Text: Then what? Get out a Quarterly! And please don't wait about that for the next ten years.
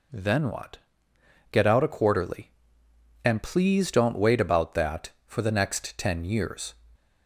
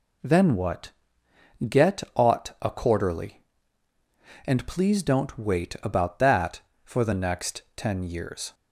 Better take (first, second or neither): first